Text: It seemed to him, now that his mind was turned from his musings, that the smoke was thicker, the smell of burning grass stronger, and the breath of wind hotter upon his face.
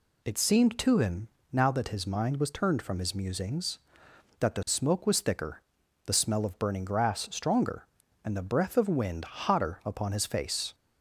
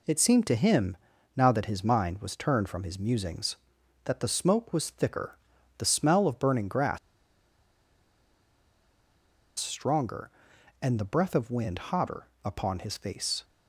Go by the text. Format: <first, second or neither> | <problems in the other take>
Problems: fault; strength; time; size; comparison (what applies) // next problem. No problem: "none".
first | pauses between "grass" and "stronger"; strong; at 6.9 s; 2.6 s long // pauses between "hotter" and "upon"; slight; at 12.2 s; 0.16 s long